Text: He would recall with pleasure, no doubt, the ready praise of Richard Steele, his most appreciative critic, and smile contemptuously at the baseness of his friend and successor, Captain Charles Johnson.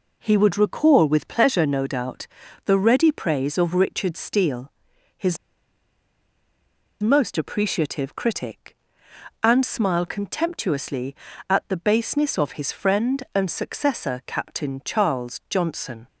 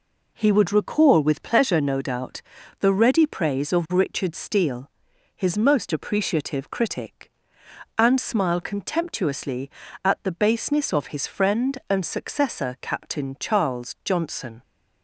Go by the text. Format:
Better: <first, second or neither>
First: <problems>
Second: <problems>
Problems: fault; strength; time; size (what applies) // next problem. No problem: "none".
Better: second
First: pauses between "his" and "most"; strong; at 5.3 s; 1.6 s long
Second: none